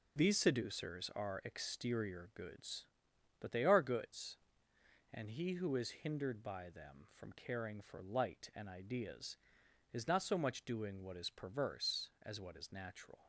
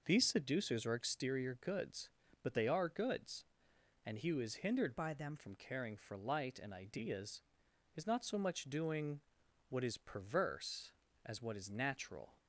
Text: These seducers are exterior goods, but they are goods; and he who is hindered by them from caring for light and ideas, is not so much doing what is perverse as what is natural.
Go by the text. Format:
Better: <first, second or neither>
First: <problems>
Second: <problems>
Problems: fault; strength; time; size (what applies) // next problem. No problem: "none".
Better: first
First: none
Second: changes voice from "by" to "them"; from 4.9 to 5.3 s; 0.4 s long // pauses between "doing" and "what"; noticeable; at 9.2 s; 0.48 s long